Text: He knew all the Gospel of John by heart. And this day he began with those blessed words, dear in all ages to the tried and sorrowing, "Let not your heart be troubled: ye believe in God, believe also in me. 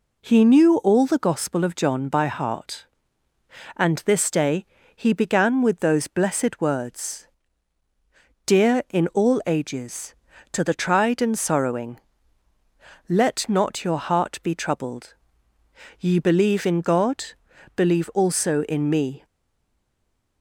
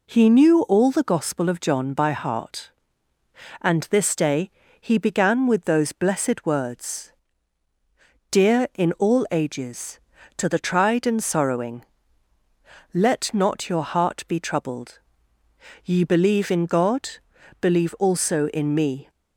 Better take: second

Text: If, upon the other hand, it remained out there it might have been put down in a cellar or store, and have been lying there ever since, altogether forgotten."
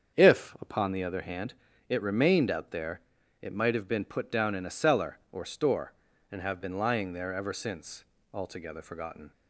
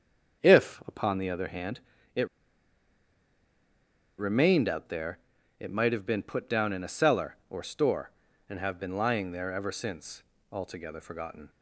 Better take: first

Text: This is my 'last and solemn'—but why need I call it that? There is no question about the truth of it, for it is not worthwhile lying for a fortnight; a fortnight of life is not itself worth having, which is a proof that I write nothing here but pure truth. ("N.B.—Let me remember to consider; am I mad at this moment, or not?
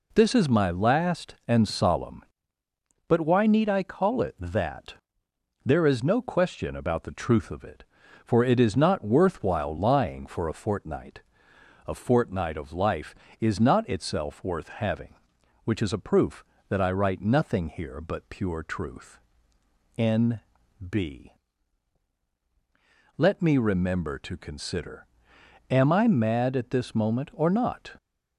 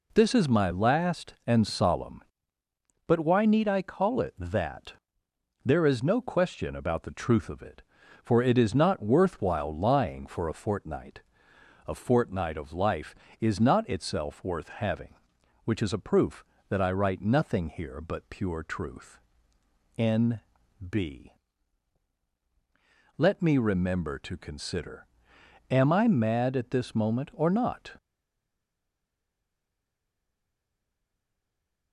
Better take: first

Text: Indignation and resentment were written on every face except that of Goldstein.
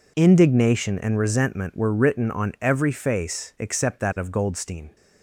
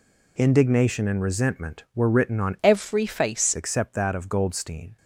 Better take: first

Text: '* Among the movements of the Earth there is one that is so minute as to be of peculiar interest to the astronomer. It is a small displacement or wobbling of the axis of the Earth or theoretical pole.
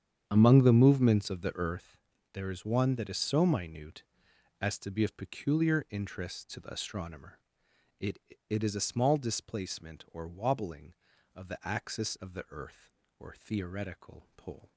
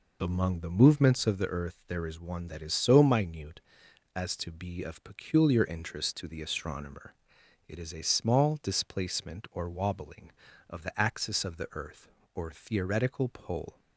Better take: second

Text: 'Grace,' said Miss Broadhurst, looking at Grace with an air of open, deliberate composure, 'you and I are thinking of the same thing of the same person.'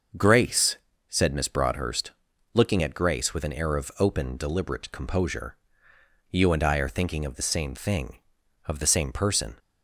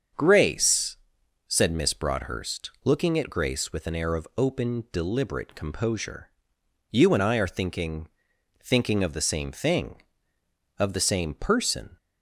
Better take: first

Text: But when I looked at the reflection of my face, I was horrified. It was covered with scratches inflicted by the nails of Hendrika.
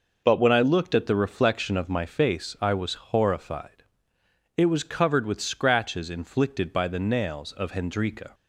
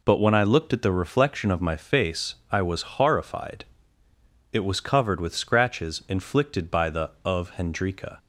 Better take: first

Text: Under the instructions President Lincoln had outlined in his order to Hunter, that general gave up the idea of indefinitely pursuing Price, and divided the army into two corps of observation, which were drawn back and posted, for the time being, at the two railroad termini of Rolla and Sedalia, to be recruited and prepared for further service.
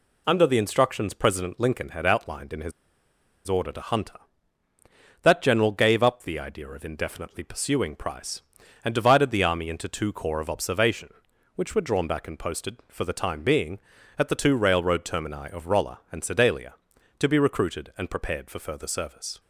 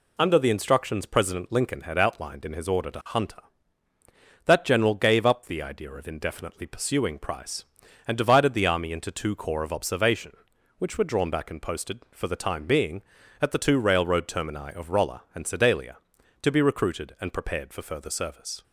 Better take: second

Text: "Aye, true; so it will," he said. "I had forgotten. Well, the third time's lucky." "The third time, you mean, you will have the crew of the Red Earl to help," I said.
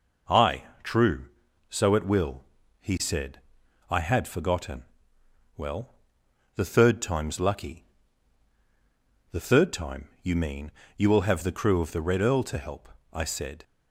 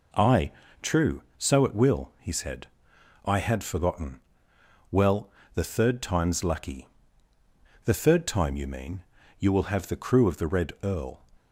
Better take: first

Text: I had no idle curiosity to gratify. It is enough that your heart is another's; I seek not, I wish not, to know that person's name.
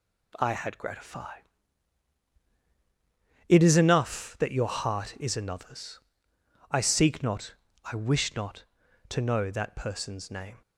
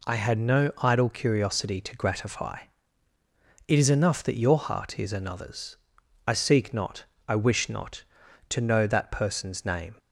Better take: second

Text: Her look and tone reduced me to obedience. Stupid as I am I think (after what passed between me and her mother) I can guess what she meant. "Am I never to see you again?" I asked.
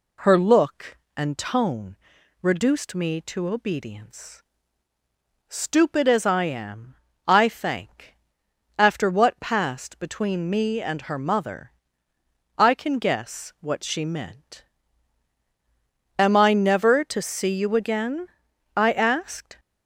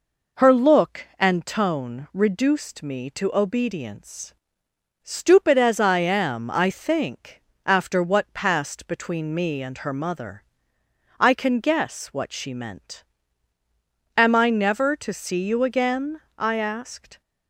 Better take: second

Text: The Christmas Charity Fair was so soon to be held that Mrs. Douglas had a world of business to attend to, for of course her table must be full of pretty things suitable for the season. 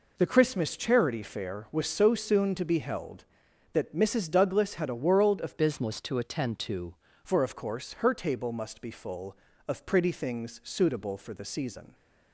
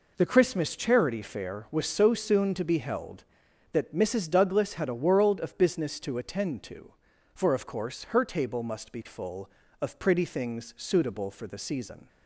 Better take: second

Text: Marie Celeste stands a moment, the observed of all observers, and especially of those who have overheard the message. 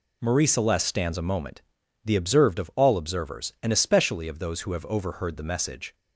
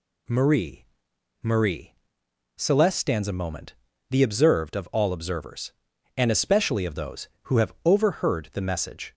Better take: first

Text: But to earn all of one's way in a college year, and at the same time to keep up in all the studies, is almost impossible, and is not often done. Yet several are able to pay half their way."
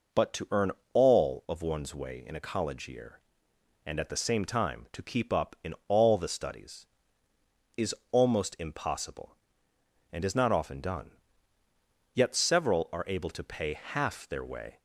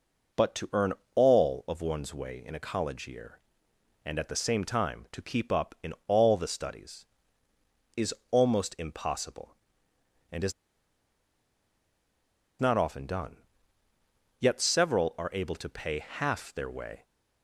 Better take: first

